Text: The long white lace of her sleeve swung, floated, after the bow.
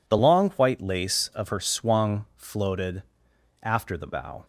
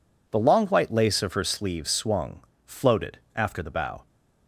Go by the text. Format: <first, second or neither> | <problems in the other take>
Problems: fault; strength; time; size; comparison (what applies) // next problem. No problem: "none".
second | skips "sleeve"; at 1.5 s